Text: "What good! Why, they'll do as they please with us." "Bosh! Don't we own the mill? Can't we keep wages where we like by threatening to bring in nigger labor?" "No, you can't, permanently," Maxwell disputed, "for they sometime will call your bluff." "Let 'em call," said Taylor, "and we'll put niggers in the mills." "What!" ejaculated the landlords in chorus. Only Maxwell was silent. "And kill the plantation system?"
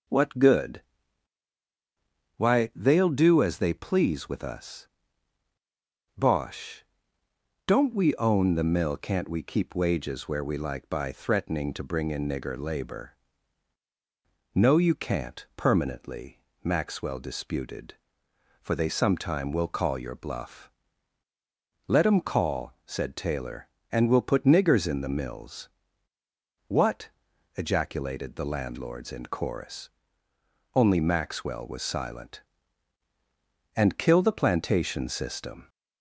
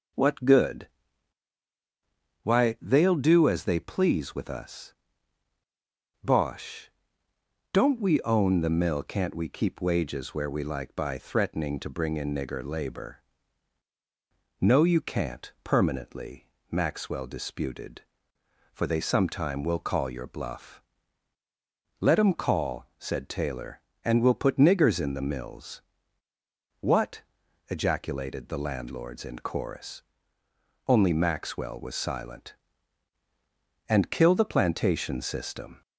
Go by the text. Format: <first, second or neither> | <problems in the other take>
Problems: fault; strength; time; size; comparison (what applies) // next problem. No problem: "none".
neither | none